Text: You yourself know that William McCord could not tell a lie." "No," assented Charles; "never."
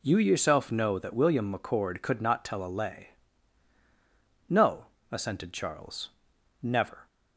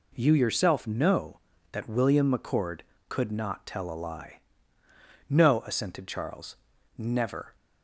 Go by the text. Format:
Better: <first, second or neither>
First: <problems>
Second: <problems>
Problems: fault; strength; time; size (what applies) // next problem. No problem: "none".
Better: second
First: says "lay" for "lie"; at 2.7 s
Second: none